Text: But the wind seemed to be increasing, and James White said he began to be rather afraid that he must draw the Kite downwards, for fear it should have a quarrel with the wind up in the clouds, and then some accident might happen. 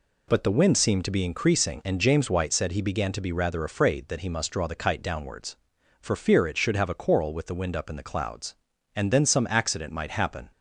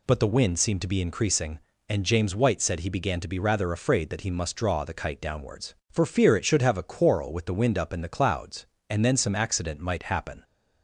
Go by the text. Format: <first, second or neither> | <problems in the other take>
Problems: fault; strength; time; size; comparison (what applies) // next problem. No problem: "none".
neither | none